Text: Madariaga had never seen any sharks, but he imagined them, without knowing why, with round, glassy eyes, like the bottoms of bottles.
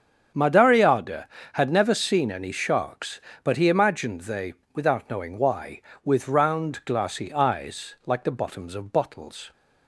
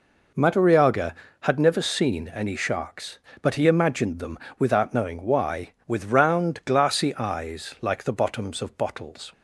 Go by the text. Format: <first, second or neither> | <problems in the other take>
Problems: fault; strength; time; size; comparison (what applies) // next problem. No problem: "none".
second | starts louder than the rest; strong; until 1.6 s; 7.5 dB // says "they" for "them"; at 4.2 s